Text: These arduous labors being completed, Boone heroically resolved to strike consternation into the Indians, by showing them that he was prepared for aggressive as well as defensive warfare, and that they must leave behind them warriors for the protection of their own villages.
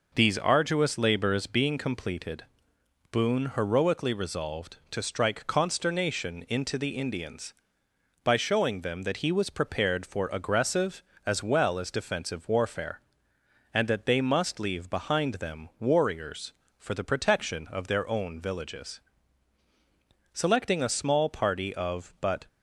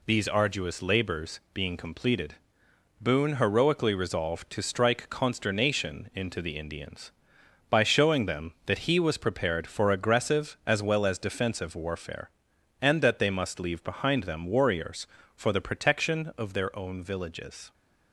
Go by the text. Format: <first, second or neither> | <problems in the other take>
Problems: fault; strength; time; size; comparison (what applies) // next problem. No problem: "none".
second | goes on to say "Selecting a small party of but"; strong; from 20.3 s on; 2.1 s long